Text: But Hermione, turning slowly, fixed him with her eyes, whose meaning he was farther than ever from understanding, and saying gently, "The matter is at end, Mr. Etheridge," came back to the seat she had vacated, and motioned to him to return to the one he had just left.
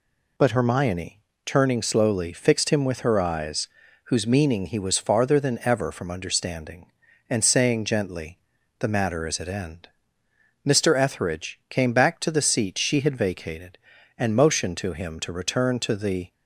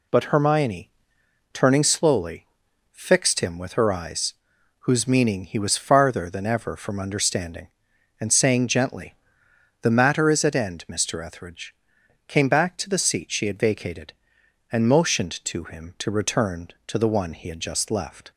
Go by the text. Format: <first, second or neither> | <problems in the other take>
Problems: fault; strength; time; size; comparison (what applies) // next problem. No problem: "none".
second | stops before "one he had just left"; at 16.3 s